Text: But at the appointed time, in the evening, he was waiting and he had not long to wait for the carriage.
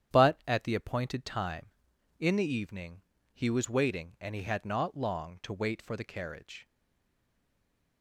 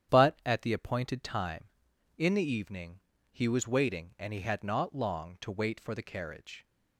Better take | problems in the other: second | starts louder than the rest; strong; until 1.1 s; 9.5 dB; strong in the second // stays silent after the last word; noticeable; from 6.6 s on; 1.4 s long

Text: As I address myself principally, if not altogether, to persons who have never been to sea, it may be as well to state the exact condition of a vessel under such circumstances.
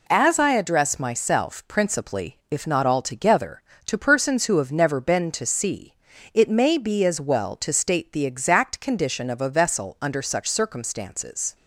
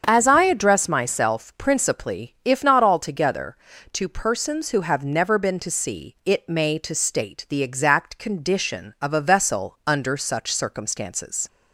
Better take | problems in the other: first | starts louder than the rest; strong; until 1.0 s; 7 dB // skips "be as well"; at 6.7 s

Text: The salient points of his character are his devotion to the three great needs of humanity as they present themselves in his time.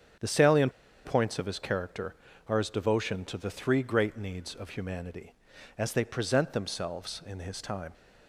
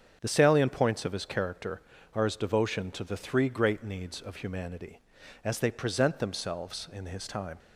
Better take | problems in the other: second | starts louder than the rest; strong; until 1.5 s; 7.5 dB; strong in the second // pauses between "salient" and "points"; slight; at 0.7 s; 0.33 s long

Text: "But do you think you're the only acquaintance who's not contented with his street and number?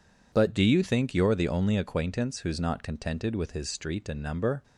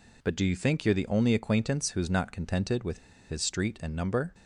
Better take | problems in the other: first | pauses between "with" and "his"; slight; at 2.9 s; 0.31 s long

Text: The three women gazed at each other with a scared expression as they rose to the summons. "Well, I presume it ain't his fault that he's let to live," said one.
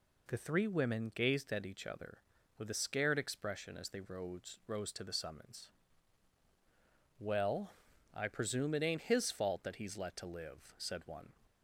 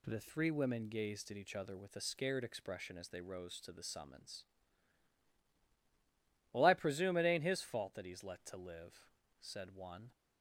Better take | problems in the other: second | says "rose" twice; at 4.6 s

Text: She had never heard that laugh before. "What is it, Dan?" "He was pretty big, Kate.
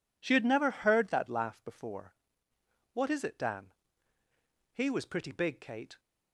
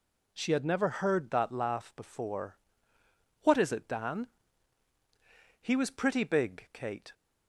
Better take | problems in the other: neither | none

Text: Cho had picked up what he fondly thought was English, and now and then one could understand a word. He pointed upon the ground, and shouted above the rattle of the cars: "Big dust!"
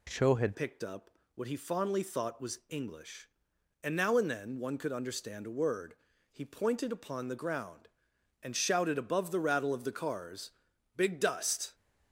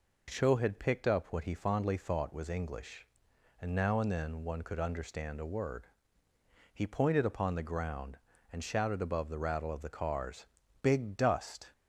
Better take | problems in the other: second | changes voice at "picked"; from 0.5 s on; 11.2 s long // pauses between "up" and "what"; slight; at 1.1 s; 0.24 s long

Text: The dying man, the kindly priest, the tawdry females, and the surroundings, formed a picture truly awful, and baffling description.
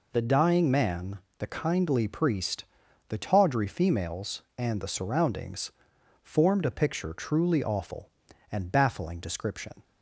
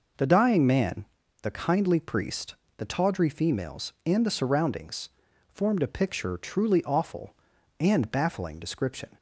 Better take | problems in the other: neither | none

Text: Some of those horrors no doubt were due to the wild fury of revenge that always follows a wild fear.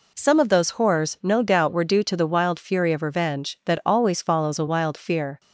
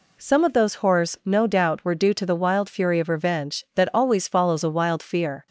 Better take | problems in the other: neither | none

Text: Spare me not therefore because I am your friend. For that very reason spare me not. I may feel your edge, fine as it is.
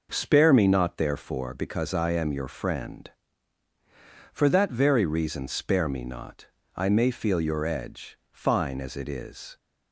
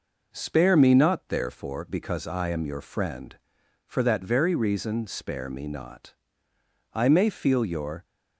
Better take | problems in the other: first | stops before "edge fine as it is"; at 8.0 s

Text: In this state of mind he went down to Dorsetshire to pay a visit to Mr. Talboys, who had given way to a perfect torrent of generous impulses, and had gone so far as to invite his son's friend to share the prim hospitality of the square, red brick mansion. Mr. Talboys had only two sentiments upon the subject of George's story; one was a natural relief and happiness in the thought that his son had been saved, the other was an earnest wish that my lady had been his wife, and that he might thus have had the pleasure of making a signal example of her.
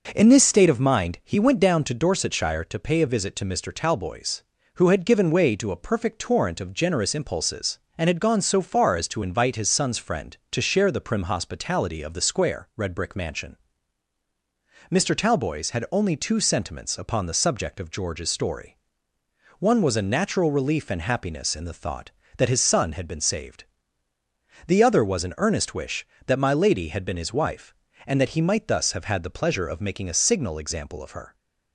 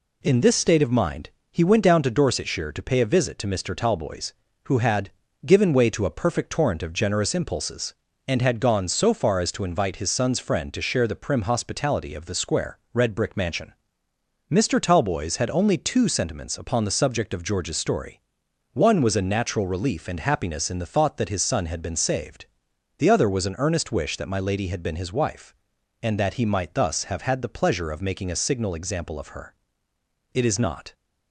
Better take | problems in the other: first | pauses between "mind" and "he"; slight; at 1.3 s; 0.20 s long // pauses between "had" and "given"; slight; at 5.1 s; 0.36 s long // goes on to say "It is not"; noticeable; from 30.3 s on; 0.62 s long

